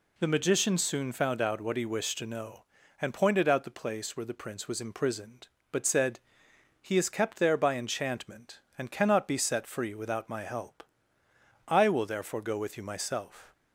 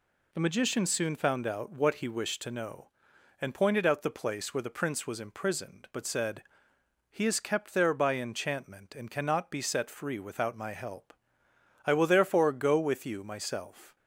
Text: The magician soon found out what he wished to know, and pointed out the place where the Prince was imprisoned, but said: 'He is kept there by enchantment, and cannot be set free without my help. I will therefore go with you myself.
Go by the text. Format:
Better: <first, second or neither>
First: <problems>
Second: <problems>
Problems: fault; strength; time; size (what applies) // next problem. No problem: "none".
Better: neither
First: none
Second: none